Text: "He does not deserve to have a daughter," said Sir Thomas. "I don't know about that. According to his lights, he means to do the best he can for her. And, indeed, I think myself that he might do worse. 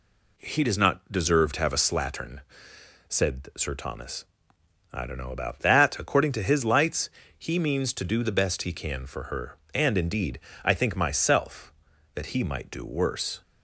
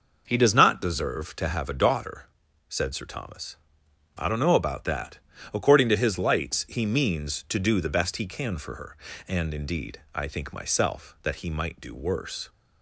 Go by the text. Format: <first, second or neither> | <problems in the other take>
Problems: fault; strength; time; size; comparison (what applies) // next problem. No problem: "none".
second | says "slattern" for "daughter"; at 1.8 s